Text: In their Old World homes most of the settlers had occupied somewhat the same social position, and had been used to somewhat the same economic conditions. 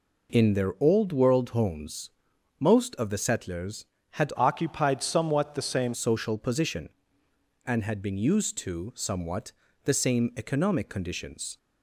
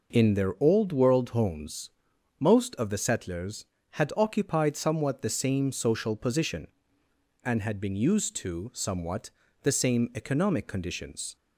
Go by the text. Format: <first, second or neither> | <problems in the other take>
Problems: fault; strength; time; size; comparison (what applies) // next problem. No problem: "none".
second | pauses between "homes" and "most"; noticeable; at 2.1 s; 0.50 s long; noticeable in the second // changes voice from "occupied" to "same"; from 4.3 to 5.9 s; 1.6 s long // pauses between "somewhat" and "the"; slight; at 9.5 s; 0.32 s long; slight in the second